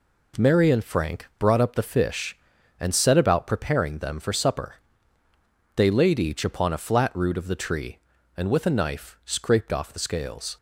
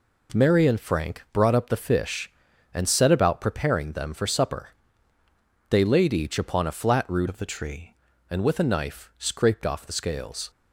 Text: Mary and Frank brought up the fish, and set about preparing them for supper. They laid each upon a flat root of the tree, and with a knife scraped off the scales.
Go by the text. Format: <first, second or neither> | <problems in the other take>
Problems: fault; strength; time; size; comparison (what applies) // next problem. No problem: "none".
first | changes voice from "of" to "tree"; from 7.2 to 7.9 s; 0.7 s long